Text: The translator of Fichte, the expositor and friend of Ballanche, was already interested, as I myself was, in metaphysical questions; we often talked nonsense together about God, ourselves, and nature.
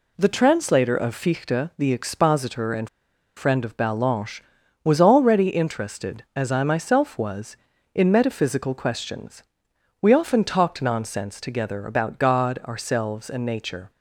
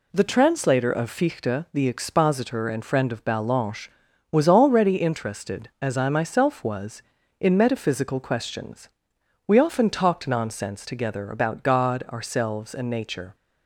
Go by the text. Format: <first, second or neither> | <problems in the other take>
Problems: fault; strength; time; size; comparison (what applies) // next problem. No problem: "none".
second | pauses between "and" and "friend"; noticeable; at 2.8 s; 0.47 s long